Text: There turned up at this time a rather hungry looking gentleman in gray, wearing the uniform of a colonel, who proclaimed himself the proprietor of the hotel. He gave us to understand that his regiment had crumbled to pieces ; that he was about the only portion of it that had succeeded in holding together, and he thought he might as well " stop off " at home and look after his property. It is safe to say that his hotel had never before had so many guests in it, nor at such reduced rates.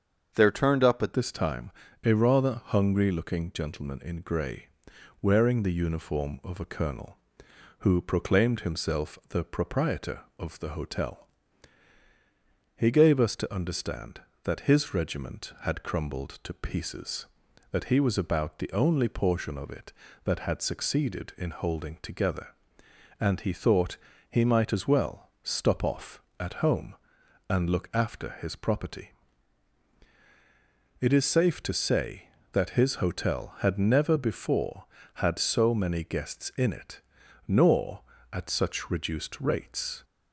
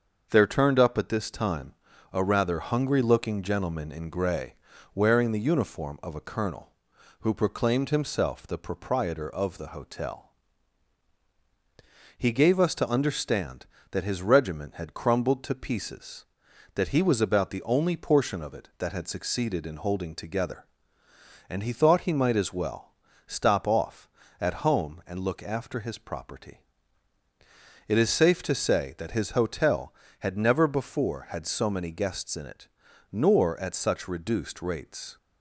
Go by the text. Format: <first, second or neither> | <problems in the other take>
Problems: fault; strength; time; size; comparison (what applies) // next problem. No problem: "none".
second | starts louder than the rest; until 1.3 s; 7 dB; also in the second // changes voice at "this"; from 1.1 s on; 38.9 s long // pauses between "time" and "a"; slight; at 1.6 s; 0.34 s long; also in the second // pauses between "thought" and "he"; slight; at 23.9 s; 0.32 s long